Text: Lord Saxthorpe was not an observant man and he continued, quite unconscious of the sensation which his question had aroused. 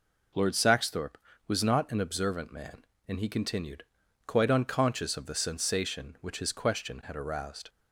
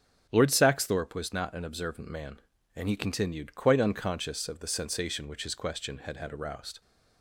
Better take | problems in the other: first | starts louder than the rest; until 1.3 s; 7 dB // says "had" twice; at 6.1 s

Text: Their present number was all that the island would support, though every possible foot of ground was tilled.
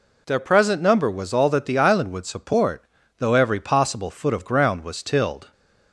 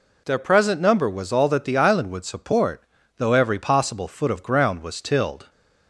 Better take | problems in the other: neither | none

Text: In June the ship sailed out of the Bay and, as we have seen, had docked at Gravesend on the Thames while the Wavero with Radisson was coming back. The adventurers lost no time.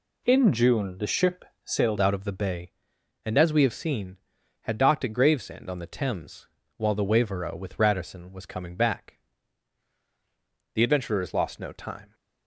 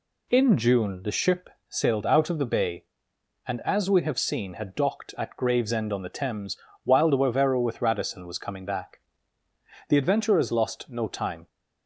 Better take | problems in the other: second | pauses between "ship" and "sailed"; slight; at 1.4 s; 0.22 s long; slight in the second // changes voice at "out"; from 2.0 s on; 10.1 s long // pauses between "Thames" and "while"; slight; at 6.4 s; 0.30 s long; slight in the second

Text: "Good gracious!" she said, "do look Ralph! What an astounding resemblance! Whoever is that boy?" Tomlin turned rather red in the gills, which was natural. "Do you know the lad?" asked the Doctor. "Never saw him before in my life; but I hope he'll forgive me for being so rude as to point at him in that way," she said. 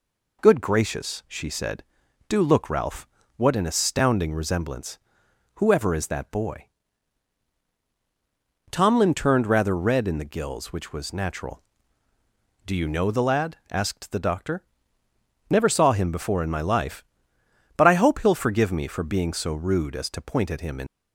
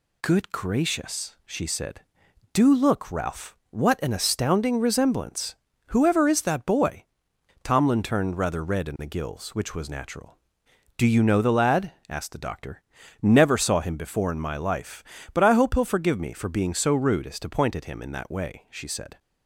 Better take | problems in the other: second | stops before "that way she said"; at 20.8 s

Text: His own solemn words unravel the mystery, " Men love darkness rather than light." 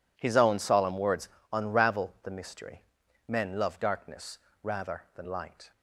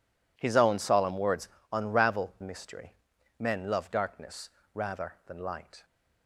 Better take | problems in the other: first | pauses between "words" and "unravel"; slight; at 1.4 s; 0.24 s long; slight in the first // skips "the"; at 2.3 s // pauses between "darkness" and "rather"; slight; at 4.5 s; 0.24 s long; slight in the first

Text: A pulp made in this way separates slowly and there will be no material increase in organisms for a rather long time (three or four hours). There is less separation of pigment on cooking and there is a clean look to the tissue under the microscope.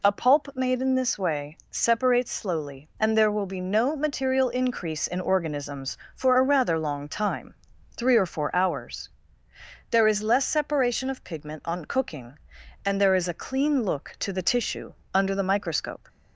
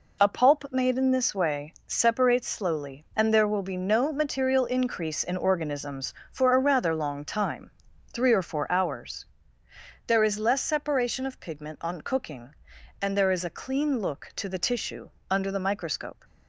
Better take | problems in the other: first | gets quieter; throughout; 7 dB // pauses between "tissue" and "under"; slight; at 15.1 s; 0.20 s long; slight in the first

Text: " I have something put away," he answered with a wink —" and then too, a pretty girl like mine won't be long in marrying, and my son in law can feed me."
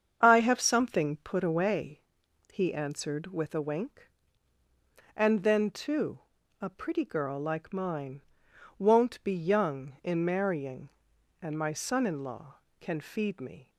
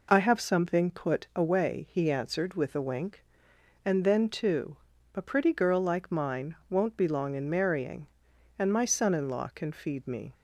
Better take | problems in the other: second | starts louder than the rest; strong; until 1.2 s; 7.5 dB // pauses between "mine" and "won't"; noticeable; at 8.2 s; 0.56 s long // says "young" for "long"; at 9.3 s

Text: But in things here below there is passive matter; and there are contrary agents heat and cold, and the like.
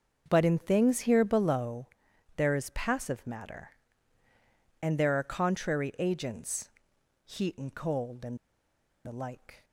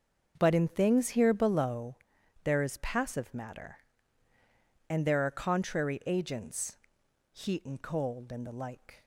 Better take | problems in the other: second | starts louder than the rest; until 1.2 s; 6.5 dB; also in the second // pauses between "below" and "there"; noticeable; at 1.8 s; 0.50 s long; noticeable in the second // pauses between "agents" and "heat"; noticeable; at 6.6 s; 0.56 s long; noticeable in the second // pauses between "and" and "the"; noticeable; at 8.3 s; 0.68 s long

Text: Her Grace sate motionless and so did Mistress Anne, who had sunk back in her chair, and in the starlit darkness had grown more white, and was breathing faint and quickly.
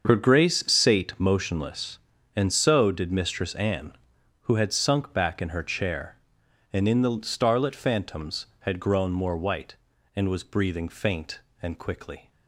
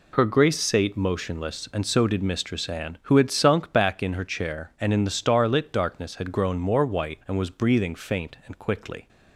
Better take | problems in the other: second | starts louder than the rest; until 1.1 s; 6.5 dB // says "phantoms" for "darkness"; at 7.7 s

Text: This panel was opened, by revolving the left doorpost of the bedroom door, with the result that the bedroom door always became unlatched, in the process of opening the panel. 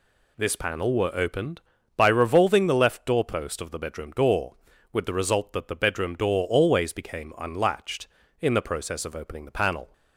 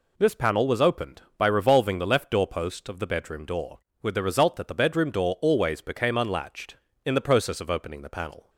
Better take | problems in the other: second | says "were" for "was"; at 0.9 s

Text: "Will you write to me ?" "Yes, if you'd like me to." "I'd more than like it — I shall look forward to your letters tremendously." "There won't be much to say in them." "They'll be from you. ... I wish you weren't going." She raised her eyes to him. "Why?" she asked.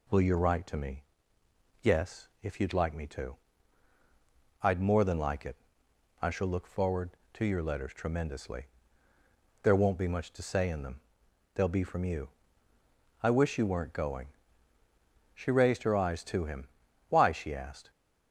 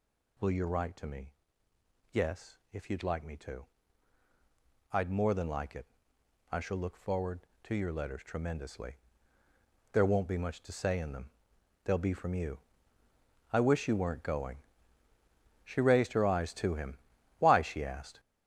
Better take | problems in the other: first | gets louder; strong; throughout; 13 dB

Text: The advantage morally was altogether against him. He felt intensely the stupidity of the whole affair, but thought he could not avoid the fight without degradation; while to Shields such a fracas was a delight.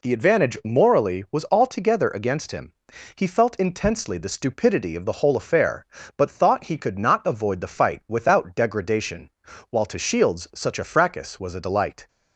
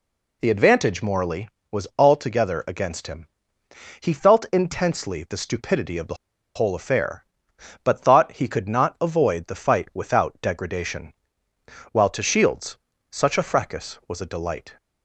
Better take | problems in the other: first | pauses between "the" and "whole"; at 6.1 s; 0.41 s long // pauses between "Shields" and "such"; slight; at 12.7 s; 0.34 s long

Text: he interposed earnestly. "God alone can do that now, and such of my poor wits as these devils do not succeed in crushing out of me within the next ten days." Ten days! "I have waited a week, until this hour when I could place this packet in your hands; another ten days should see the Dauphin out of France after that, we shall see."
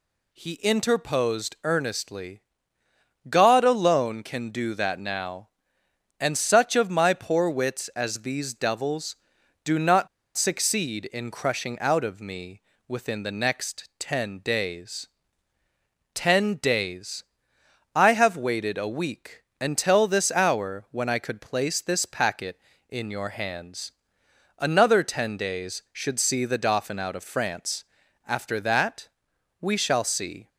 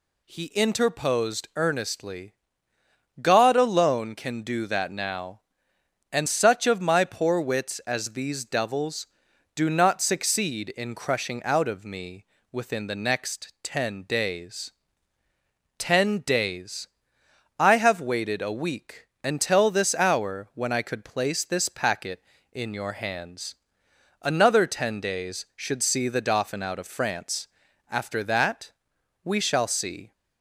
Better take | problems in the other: second | pauses between "not" and "succeed"; slight; at 10.0 s; 0.28 s long // pauses between "me" and "within"; slight; at 12.6 s; 0.26 s long; slight in the second // pauses between "France" and "after"; at 27.8 s; 0.42 s long; also in the second

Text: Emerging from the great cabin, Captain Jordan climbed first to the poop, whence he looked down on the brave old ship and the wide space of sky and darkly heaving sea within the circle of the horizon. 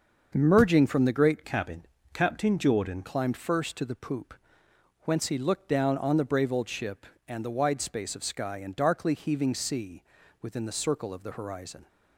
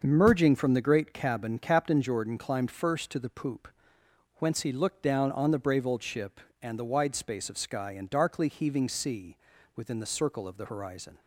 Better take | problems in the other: second | starts louder than the rest; until 1.3 s; 6.5 dB; also in the second // changes voice from "cabin" to "Jordan"; from 1.4 to 3.0 s; 1.6 s long // pauses between "sea" and "within"; at 10.0 s; 0.40 s long; also in the second

